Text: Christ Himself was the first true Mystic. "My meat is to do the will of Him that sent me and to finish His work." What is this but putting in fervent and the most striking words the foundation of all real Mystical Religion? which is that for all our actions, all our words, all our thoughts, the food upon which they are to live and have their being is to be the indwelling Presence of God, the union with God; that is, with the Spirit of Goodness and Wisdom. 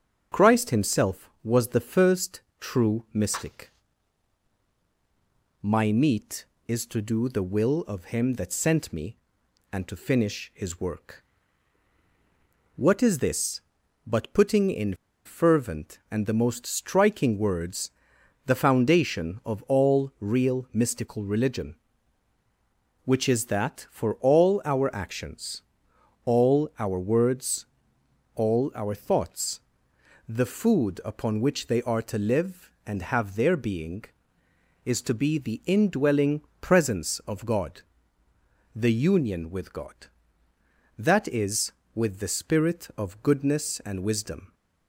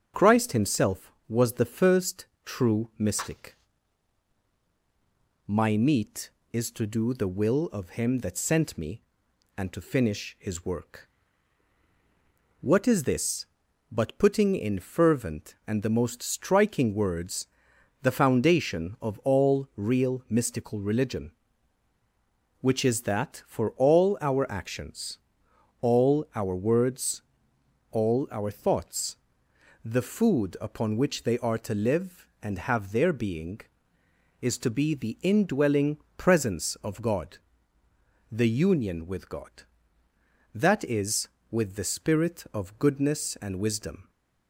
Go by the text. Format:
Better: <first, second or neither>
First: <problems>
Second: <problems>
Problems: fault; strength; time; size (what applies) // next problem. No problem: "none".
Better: second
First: starts louder than the rest; strong; until 1.4 s; 7.5 dB // pauses between "first" and "true"; slight; at 2.4 s; 0.18 s long // pauses between "in" and "fervent"; slight; at 14.9 s; 0.30 s long // pauses between "words" and "the"; noticeable; at 17.8 s; 0.56 s long // pauses between "indwelling" and "Presence"; slight; at 36.4 s; 0.20 s long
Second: starts louder than the rest; strong; until 1.3 s; 7.5 dB // pauses between "first" and "true"; slight; at 2.2 s; 0.18 s long // pauses between "words" and "the"; noticeable; at 17.4 s; 0.56 s long // pauses between "indwelling" and "Presence"; slight; at 35.9 s; 0.20 s long